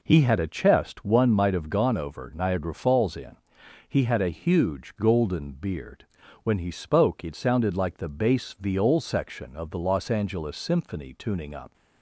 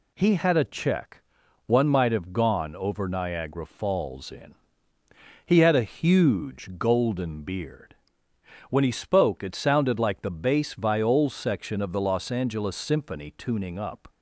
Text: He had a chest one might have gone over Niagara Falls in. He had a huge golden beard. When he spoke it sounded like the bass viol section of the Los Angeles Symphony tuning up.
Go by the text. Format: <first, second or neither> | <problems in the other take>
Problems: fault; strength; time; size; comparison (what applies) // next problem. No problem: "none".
first | says "check" for "chest"; at 0.6 s